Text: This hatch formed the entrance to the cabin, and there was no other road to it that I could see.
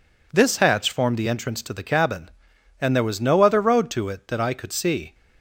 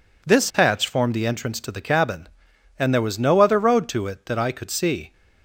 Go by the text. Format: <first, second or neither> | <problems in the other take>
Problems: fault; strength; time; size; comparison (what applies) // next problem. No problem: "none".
neither | none